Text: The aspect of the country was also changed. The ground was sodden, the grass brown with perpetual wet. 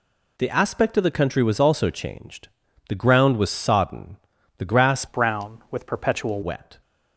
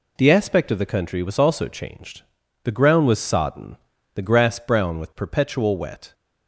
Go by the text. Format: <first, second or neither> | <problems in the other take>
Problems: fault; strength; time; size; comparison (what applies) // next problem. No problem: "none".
second | changes voice from "brown" to "perpetual"; from 5.0 to 6.4 s; 1.4 s long